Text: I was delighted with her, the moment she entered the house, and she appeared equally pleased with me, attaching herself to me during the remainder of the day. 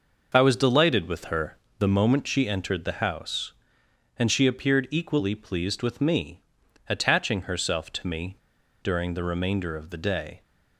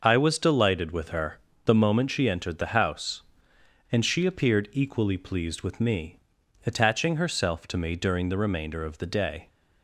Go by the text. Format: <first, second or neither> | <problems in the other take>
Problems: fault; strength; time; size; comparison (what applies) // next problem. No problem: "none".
second | pauses between "me" and "during"; at 8.3 s; 0.45 s long